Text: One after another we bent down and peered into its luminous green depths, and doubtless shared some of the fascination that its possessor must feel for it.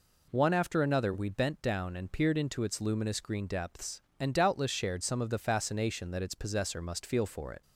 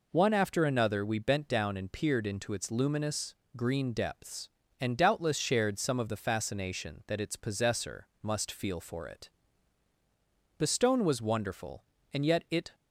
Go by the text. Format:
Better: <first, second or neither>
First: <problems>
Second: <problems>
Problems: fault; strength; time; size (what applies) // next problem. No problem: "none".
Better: first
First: none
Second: pauses between "luminous" and "green"; slight; at 3.3 s; 0.20 s long // pauses between "possessor" and "must"; slight; at 8.0 s; 0.16 s long // goes on to say "The stone was wonderful and yet it"; strong; from 10.5 s on; 2.1 s long